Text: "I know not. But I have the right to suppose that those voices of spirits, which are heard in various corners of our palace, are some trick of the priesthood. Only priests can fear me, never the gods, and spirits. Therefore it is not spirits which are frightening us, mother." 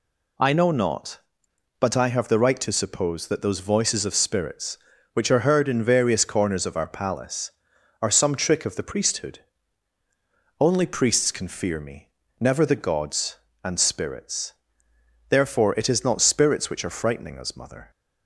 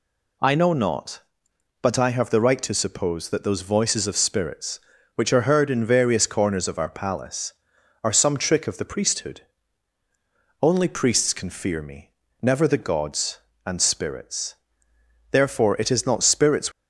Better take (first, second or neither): first